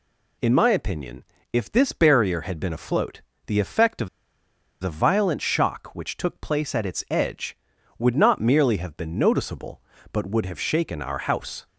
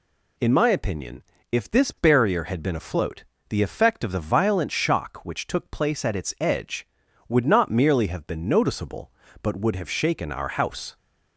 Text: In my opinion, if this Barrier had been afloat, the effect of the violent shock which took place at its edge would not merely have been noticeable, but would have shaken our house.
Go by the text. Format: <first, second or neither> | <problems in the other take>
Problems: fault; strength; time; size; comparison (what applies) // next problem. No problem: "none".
second | pauses between "of" and "the"; noticeable; at 4.0 s; 0.73 s long